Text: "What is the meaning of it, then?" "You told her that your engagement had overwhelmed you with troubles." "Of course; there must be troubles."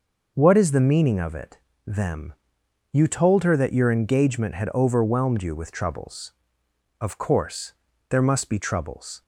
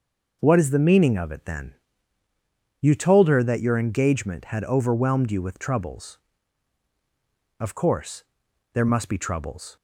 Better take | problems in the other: second | says "them" for "then"; at 1.8 s

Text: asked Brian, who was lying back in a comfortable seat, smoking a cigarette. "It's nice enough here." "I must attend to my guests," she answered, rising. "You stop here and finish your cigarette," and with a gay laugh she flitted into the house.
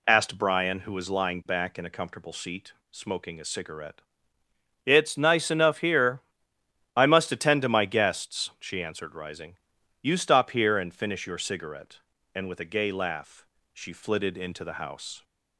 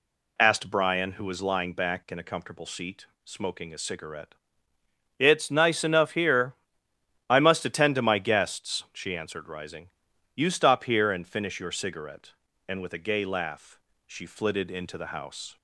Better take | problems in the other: neither | pauses between "laugh" and "she"; slight; the same in both

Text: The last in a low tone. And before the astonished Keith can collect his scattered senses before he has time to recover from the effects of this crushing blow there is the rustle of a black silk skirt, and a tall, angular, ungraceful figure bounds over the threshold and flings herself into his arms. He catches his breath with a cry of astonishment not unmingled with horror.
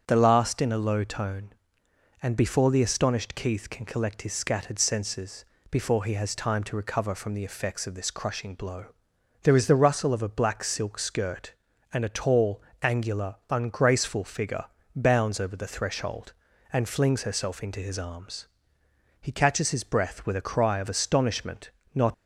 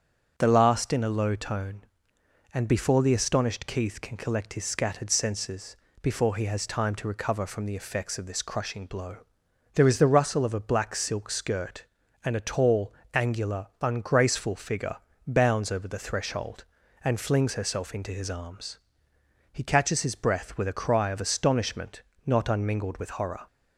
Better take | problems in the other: second | starts louder than the rest; until 1.0 s; 7 dB; also in the second // pauses between "senses" and "before"; slight; at 5.4 s; 0.26 s long; slight in the second // pauses between "blow" and "there"; noticeable; at 8.8 s; 0.58 s long; noticeable in the second // pauses between "figure" and "bounds"; slight; at 14.6 s; 0.30 s long; slight in the second // pauses between "astonishment" and "not"; slight; at 21.6 s; 0.24 s long; slight in the second // stops before "unmingled with horror"; at 22.1 s

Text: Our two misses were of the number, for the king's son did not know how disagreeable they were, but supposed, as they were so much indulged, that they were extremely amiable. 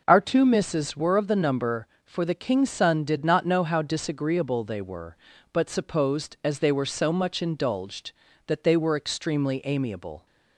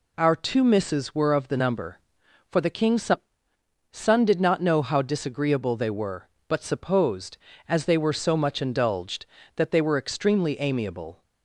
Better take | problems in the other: first | says "son" twice; at 3.9 s

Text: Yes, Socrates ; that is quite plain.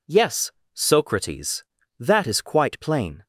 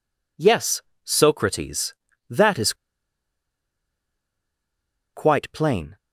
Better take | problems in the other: first | pauses between "is" and "quite"; strong; at 2.7 s; 2.4 s long

